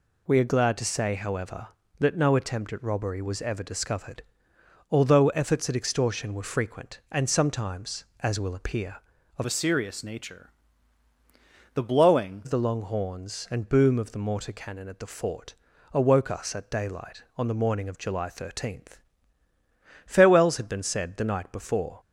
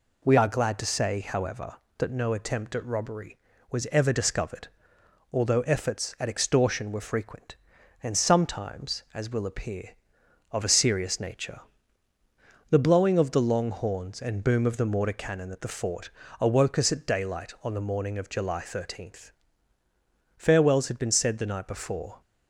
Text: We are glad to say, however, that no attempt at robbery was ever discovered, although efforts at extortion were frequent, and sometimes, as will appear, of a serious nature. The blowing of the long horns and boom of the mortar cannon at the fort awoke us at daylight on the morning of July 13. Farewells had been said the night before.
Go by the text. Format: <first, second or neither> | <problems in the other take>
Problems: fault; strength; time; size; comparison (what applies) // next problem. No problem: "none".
second | changes voice from "a" to "blowing"; from 9.4 to 12.4 s; 3.0 s long // pauses between "fort" and "awoke"; at 15.5 s; 0.40 s long; slight in the second